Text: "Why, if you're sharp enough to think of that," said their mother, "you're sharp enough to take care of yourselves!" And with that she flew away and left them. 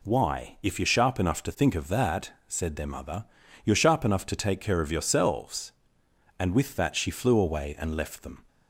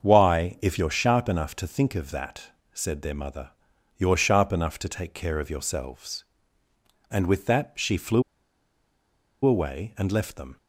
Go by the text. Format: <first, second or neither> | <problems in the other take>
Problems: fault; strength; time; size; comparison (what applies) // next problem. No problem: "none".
first | starts louder than the rest; until 1.0 s; 6.5 dB // pauses between "flew" and "away"; at 8.2 s; 1.2 s long